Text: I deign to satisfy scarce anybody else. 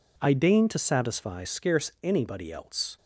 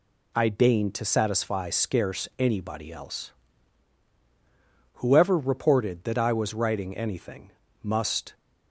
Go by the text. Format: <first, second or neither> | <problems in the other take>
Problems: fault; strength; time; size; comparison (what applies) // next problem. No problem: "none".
first | goes on to say "Whoever reported that I was writing anything must"; strong; from 4.9 s on; 3.3 s long